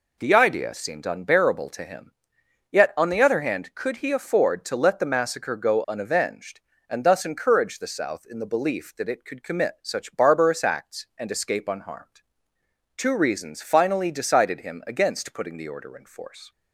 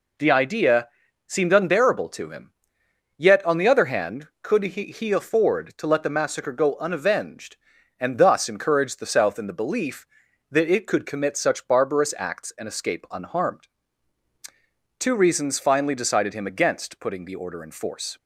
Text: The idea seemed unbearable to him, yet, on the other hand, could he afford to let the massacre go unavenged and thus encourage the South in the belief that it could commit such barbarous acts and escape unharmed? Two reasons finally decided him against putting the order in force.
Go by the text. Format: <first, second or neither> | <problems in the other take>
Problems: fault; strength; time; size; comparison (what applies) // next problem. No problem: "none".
first | pauses between "idea" and "seemed"; at 0.8 s; 0.40 s long // says "he" twice; at 4.8 s